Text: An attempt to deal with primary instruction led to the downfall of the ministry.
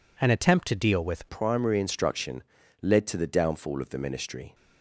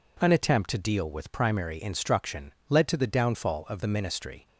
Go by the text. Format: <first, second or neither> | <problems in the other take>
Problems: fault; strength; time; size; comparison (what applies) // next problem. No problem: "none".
second | changes voice at "primary"; from 1.2 s on; 3.3 s long // pauses between "instruction" and "led"; at 2.4 s; 0.40 s long; slight in the second